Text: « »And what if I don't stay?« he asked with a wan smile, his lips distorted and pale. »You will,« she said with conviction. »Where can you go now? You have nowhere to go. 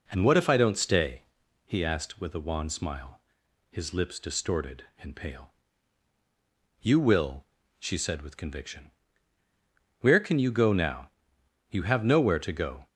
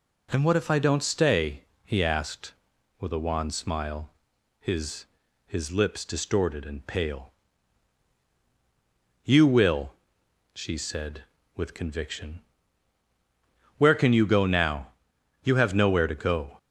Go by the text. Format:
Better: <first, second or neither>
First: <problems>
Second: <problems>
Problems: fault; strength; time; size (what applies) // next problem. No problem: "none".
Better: first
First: none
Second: says "his" twice; at 5.4 s